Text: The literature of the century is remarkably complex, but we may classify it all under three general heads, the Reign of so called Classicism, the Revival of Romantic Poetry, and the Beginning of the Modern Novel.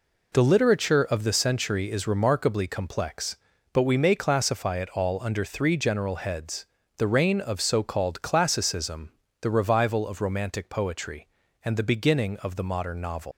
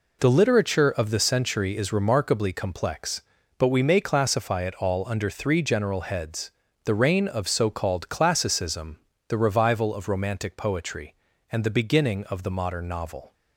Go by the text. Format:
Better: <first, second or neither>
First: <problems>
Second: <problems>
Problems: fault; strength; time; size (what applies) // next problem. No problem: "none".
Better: second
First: leaves "Novel" unfinished; at 13.3 s; 150 ms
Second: none